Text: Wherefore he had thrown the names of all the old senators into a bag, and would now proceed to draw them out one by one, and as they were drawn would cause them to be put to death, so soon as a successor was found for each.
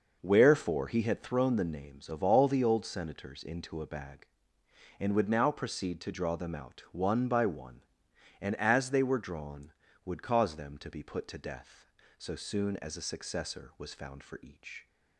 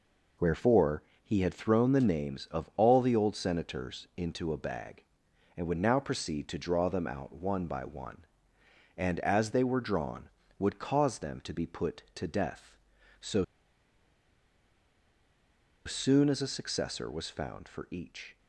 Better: first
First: none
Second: pauses between "Wherefore" and "he"; slight; at 1.0 s; 0.22 s long // pauses between "so" and "soon"; strong; at 13.4 s; 2.4 s long

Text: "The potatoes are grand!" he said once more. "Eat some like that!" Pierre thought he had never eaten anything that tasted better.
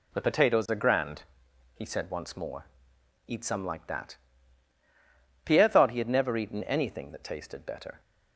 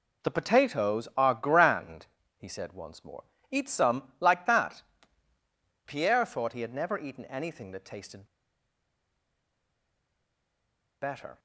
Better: first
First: none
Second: pauses between "tasted" and "better"; strong; at 8.2 s; 2.7 s long

